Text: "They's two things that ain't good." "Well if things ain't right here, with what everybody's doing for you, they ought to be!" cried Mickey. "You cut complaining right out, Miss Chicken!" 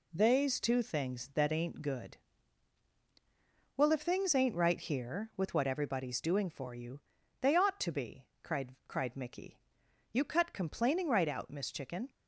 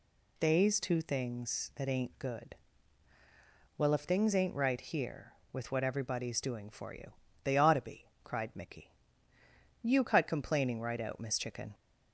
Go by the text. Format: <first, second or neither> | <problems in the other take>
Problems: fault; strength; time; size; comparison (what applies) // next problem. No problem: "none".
second | says "cried" twice; at 8.8 s